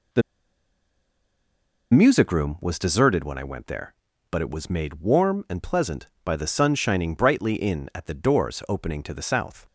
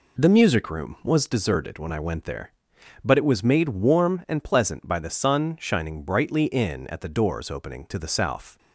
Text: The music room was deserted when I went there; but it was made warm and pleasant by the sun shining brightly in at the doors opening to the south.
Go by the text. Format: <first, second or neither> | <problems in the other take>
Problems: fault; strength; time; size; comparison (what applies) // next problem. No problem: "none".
second | pauses between "The" and "music"; strong; at 0.2 s; 1.7 s long